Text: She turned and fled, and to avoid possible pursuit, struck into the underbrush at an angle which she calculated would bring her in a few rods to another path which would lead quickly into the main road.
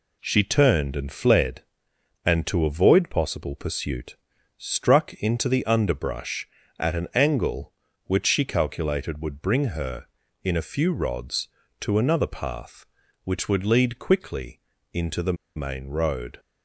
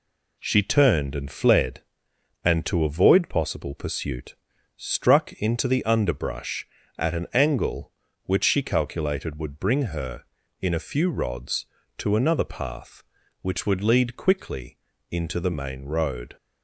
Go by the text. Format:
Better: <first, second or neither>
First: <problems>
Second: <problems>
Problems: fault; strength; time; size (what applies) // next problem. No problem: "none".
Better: second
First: pauses between "quickly" and "into"; slight; at 14.5 s; 0.32 s long // pauses between "the" and "main"; slight; at 15.3 s; 0.22 s long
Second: pauses between "quickly" and "into"; slight; at 14.7 s; 0.32 s long